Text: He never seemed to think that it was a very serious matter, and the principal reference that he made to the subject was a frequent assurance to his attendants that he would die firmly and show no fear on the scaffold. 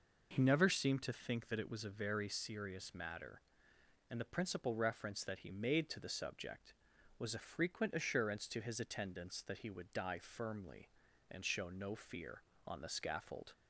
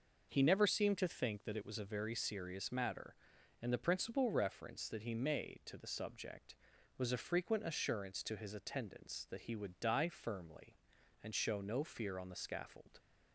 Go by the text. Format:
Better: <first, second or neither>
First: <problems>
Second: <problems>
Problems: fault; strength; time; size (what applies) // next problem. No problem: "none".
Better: neither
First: none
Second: none